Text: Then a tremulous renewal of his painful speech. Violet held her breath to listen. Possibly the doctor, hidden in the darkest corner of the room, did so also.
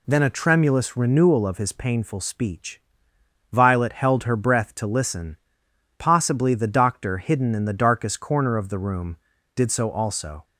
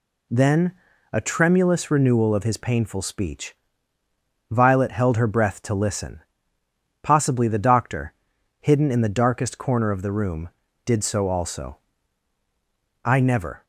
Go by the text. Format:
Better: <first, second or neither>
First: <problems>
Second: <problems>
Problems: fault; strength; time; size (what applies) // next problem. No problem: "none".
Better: first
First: none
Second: pauses between "Then" and "a"; at 0.7 s; 0.40 s long // goes on to say "I never"; from 13.0 s on; 0.60 s long